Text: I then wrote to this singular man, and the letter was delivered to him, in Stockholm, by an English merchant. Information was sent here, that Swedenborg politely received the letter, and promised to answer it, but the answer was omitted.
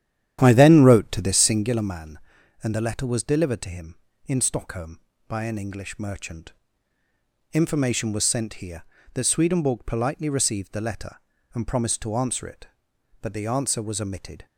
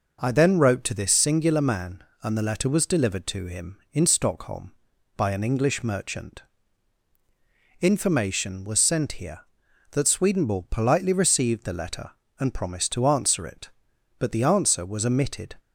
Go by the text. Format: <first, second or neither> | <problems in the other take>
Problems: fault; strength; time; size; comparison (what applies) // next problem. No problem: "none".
second | starts louder than the rest; strong; until 1.7 s; 10.5 dB